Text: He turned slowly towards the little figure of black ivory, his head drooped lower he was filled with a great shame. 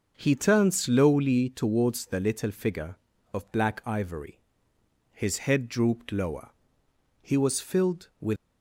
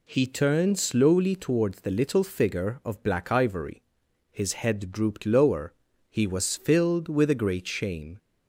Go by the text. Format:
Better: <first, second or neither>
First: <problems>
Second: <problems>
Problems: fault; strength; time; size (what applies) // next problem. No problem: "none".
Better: second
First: pauses between "lower" and "he"; noticeable; at 6.5 s; 0.70 s long // stops before "a great shame"; at 8.3 s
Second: pauses between "lower" and "he"; slight; at 5.7 s; 0.36 s long